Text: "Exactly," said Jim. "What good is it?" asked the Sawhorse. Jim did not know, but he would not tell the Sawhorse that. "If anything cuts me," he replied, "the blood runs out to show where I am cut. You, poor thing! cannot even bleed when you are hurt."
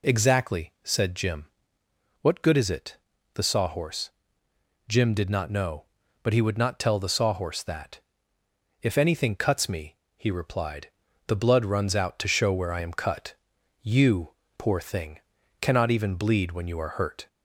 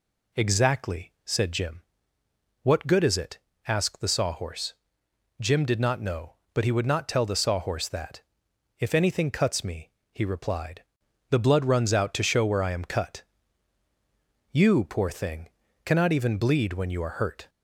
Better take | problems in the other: second | skips "asked"; at 3.1 s

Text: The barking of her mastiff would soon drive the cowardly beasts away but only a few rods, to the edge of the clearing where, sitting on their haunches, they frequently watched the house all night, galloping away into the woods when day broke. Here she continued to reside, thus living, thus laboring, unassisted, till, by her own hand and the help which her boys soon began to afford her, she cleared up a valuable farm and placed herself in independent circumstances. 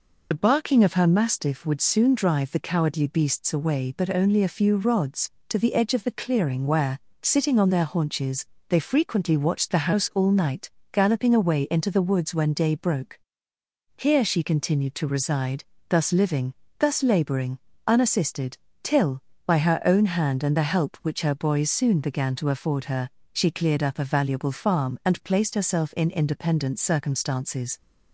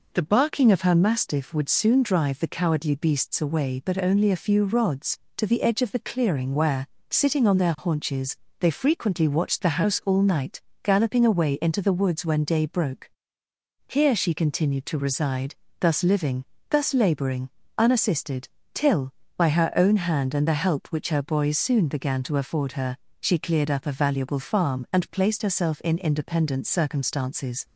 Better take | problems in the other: second | loses the start of "The"; at 0.3 s; 45 ms

